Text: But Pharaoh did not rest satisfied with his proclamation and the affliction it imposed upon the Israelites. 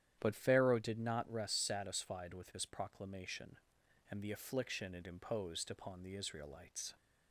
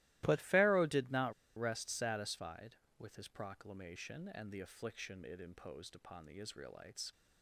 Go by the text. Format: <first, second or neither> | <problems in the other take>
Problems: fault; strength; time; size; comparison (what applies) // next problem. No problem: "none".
first | starts louder than the rest; strong; until 1.2 s; 17 dB; strong in the first // pauses between "not" and "rest"; slight; at 1.3 s; 0.26 s long